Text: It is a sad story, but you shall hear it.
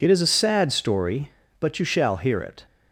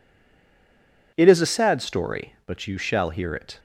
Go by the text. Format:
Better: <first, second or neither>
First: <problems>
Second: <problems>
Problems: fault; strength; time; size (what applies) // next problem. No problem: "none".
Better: first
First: none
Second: stays silent before the first word; until 1.1 s; 1.1 s long